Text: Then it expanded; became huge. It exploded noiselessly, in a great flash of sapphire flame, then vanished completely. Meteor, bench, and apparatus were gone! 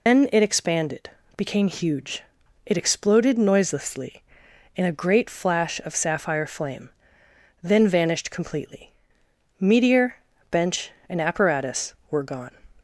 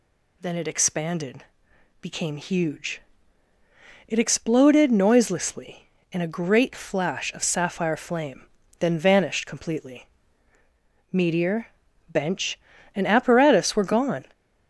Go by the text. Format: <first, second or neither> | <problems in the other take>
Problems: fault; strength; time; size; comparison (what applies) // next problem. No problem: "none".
second | loses the start of "Then"; at 0.0 s; 170 ms